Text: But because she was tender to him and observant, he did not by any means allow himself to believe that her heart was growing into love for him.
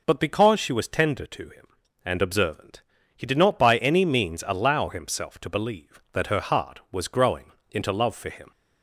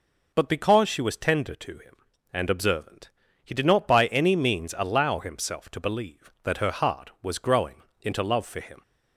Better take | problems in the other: neither | pauses between "growing" and "into"; slight; the same in both

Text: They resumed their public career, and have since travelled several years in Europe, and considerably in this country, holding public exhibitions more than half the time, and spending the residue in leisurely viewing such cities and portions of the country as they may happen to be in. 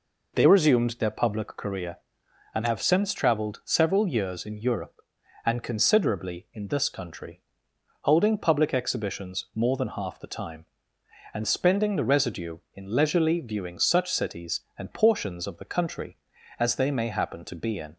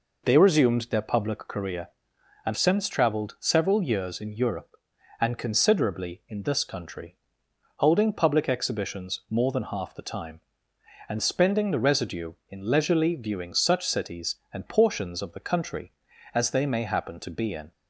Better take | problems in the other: first | skips "have"; at 2.5 s

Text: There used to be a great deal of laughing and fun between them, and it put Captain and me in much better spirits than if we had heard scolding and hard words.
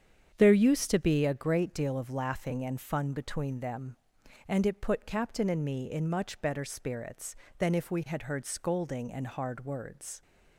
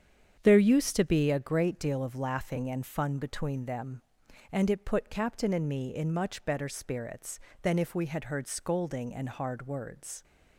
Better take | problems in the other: neither | starts louder than the rest; strong; the same in both

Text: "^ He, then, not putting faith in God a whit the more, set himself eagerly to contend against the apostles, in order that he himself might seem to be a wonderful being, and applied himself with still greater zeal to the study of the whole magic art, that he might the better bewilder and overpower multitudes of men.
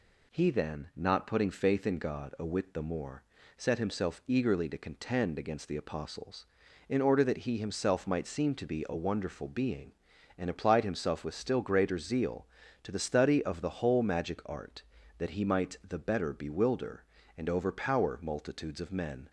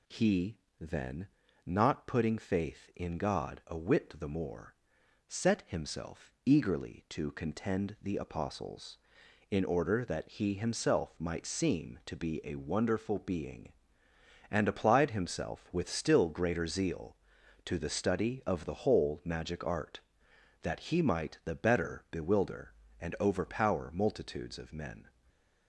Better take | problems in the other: first | skips "against"; at 7.9 s // stays silent after the last word; slight; from 25.0 s on; 0.6 s long

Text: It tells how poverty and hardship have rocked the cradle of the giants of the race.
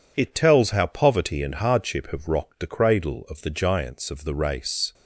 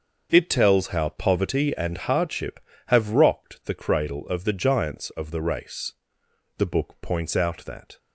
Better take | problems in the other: first | starts louder than the rest; until 1.3 s; 6.5 dB // goes on to say "The book points out that"; from 6.5 s on; 1.4 s long

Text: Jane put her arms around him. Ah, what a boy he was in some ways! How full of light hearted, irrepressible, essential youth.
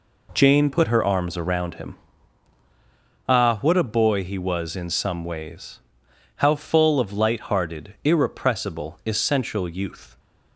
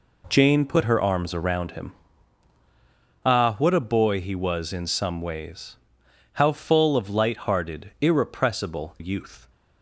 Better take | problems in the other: first | skips "essential"; at 8.9 s

